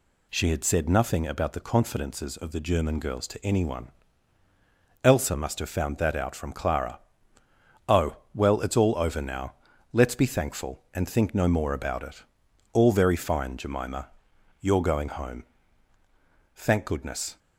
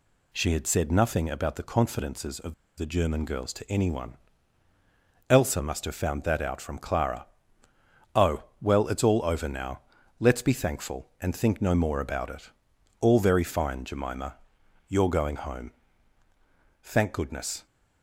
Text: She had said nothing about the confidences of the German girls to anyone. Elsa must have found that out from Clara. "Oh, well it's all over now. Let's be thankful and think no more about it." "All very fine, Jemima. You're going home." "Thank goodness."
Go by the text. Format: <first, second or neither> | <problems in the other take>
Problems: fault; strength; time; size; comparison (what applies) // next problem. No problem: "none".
first | pauses between "of" and "the"; slight; at 2.5 s; 0.23 s long